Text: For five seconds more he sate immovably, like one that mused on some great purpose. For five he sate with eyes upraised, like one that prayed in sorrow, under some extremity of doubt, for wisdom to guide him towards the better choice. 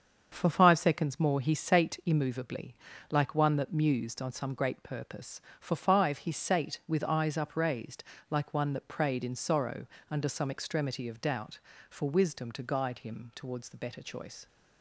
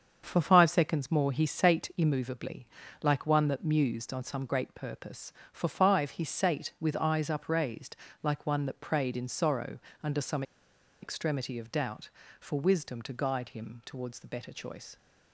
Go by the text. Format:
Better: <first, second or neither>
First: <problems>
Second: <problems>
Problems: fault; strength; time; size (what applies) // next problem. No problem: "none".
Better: first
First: starts louder than the rest; until 1.3 s; 7 dB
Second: starts louder than the rest; until 1.2 s; 7 dB // pauses between "some" and "extremity"; noticeable; at 10.4 s; 0.60 s long